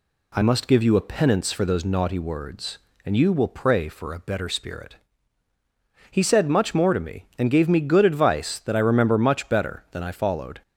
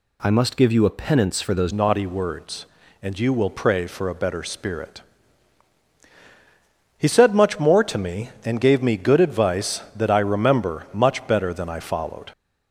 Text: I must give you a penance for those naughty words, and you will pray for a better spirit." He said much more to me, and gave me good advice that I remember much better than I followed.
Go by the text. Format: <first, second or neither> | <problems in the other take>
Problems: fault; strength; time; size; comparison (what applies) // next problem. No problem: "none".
first | changes voice at "naughty"; from 1.7 s on; 10.5 s long